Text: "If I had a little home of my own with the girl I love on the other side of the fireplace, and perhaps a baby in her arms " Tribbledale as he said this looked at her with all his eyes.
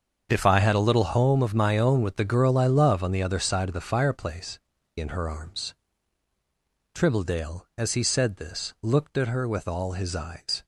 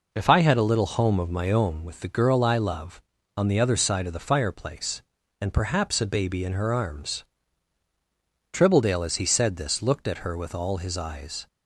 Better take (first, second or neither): second